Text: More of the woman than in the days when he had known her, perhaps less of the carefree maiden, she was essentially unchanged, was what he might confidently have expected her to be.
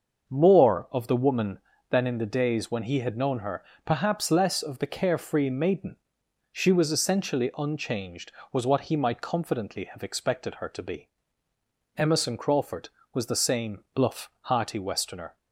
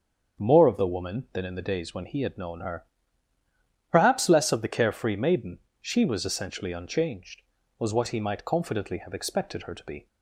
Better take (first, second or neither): second